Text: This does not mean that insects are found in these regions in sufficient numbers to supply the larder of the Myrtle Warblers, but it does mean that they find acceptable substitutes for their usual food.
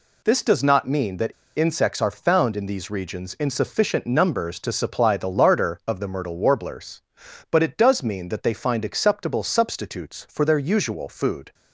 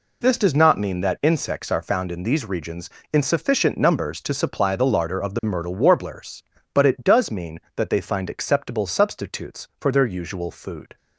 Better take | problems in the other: second | pauses between "that" and "insects"; slight; at 1.3 s; 0.24 s long

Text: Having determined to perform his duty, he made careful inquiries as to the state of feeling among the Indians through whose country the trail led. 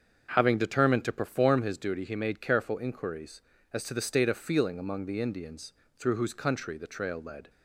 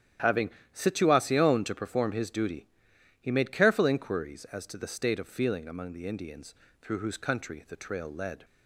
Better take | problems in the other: first | starts louder than the rest; strong; until 1.4 s; 11 dB; also in the first // says "situacion" for "determined"; at 0.7 s // pauses between "Indians" and "through"; slight; at 6.5 s; 0.30 s long; slight in the first

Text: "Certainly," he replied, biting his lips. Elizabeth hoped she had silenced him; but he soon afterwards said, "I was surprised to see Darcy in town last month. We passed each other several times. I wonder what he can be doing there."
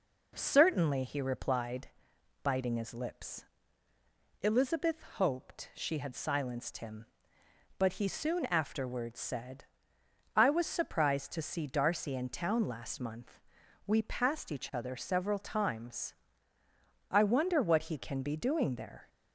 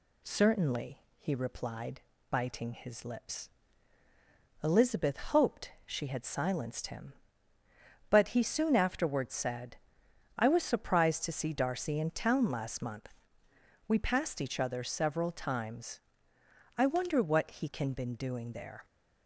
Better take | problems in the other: first | says "been" for "be"; at 17.9 s

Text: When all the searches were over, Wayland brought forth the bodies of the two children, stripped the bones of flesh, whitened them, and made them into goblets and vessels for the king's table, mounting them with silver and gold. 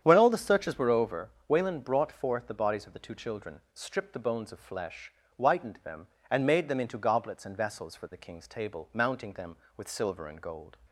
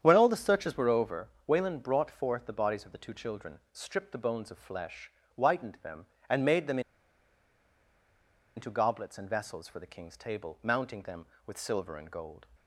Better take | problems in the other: first | starts louder than the rest; strong; until 1.0 s; 9 dB; strong in the first // pauses between "them" and "into"; strong; at 6.7 s; 1.7 s long

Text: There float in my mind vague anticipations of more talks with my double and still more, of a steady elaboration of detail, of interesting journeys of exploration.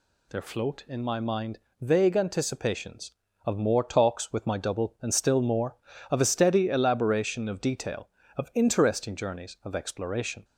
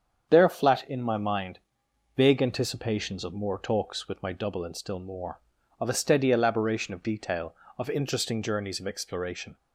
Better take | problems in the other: first | starts louder than the rest; strong; until 1.3 s; 7.5 dB // says "flat" for "float"; at 0.4 s // pauses between "mind" and "vague"; noticeable; at 1.5 s; 0.56 s long; slight in the first

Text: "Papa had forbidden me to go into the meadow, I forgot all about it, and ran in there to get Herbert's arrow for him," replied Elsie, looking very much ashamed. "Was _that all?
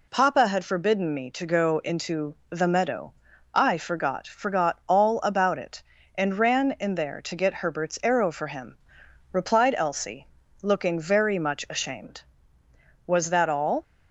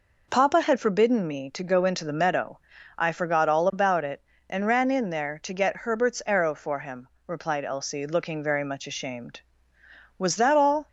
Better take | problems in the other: second | says "forgot" twice; at 4.2 s

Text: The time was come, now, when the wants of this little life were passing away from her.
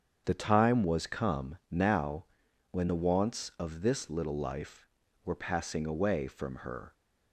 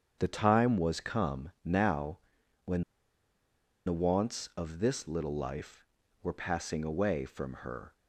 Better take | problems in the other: first | starts louder than the rest; strong; until 1.2 s; 7.5 dB; strong in the first // pauses between "when" and "the"; at 2.8 s; 1.0 s long

